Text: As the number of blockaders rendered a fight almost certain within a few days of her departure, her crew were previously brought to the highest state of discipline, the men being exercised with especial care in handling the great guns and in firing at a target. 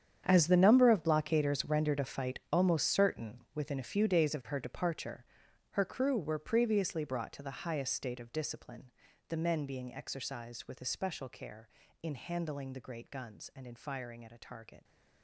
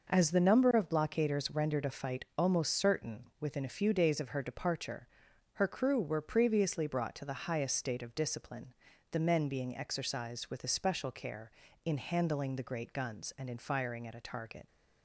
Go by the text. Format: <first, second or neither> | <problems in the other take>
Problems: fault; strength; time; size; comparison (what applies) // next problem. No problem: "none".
second | gets quieter; strong; throughout; 15.5 dB